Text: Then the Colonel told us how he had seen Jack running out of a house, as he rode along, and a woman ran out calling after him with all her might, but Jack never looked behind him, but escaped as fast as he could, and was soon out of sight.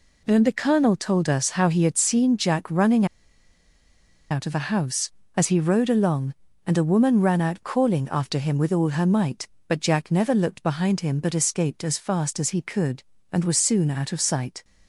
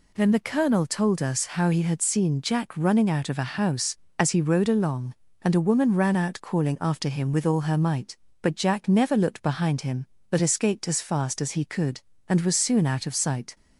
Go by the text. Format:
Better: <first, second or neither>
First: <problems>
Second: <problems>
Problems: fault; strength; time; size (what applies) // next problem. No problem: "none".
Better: second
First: pauses between "running" and "out"; strong; at 3.0 s; 1.2 s long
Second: none